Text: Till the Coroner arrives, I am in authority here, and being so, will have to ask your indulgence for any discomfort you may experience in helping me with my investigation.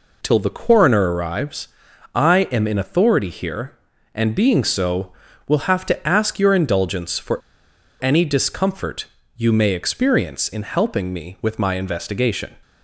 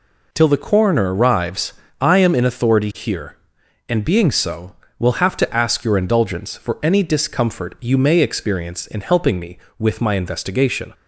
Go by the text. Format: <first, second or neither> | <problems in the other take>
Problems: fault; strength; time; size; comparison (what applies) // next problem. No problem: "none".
second | pauses between "for" and "any"; noticeable; at 7.3 s; 0.61 s long // pauses between "discomfort" and "you"; slight; at 9.0 s; 0.32 s long